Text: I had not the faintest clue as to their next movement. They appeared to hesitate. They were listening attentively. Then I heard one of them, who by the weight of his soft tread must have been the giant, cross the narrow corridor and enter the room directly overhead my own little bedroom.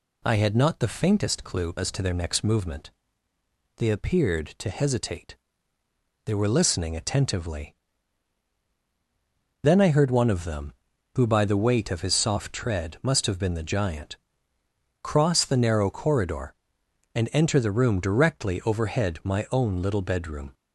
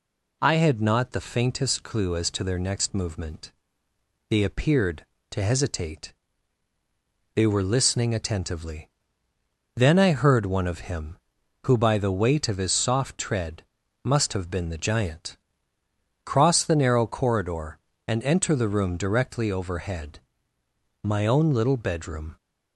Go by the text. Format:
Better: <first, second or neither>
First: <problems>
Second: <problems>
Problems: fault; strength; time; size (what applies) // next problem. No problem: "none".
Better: first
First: none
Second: says "him" for "them"; at 10.9 s // pauses between "tread" and "must"; at 13.6 s; 0.42 s long // pauses between "overhead" and "my"; noticeable; at 20.2 s; 0.82 s long